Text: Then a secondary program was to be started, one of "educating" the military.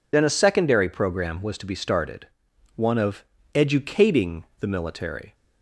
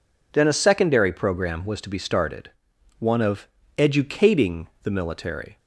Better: second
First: loses the start of "Then"; at 0.1 s; 30 ms // pauses between "of" and "educating"; slight; at 3.2 s; 0.28 s long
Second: pauses between "of" and "educating"; slight; at 3.4 s; 0.28 s long

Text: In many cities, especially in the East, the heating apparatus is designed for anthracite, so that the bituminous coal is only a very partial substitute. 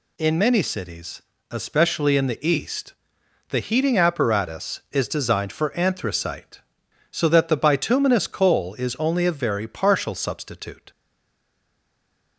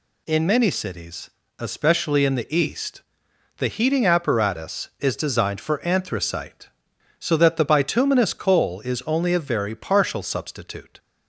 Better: second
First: stays silent after the last word; noticeable; from 10.9 s on; 1.4 s long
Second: none

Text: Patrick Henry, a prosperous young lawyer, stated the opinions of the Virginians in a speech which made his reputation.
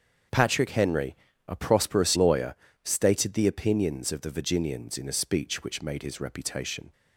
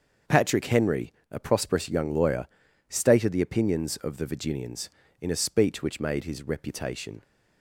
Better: second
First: starts louder than the rest; until 1.6 s; 7 dB // skips "young"; at 2.1 s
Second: starts louder than the rest; until 1.4 s; 6.5 dB

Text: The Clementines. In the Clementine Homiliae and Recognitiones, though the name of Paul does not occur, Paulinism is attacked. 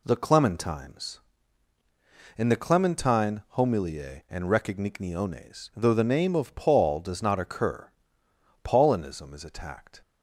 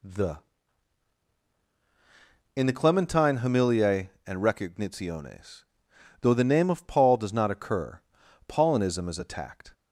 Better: first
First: none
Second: skips "Clementines"; at 1.4 s

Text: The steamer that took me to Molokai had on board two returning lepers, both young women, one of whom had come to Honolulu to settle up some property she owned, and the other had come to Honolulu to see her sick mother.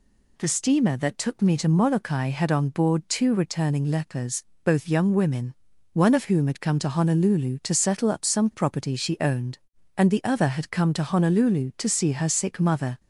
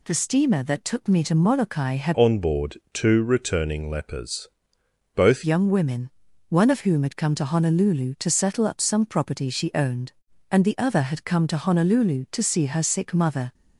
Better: first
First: none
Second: changes voice from "on" to "both"; from 2.1 to 5.4 s; 3.3 s long

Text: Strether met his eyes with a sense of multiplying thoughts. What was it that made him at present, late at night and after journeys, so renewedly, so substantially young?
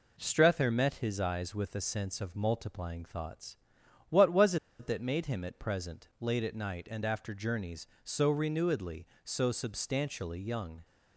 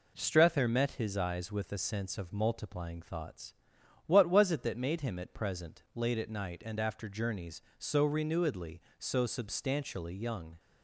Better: second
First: pauses between "was" and "it"; slight; at 4.5 s; 0.23 s long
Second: none

